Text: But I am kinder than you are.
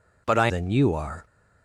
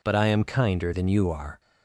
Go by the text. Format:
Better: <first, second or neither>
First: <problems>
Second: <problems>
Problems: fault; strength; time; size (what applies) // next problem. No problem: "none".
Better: second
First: skips "am kinder"; at 0.4 s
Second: none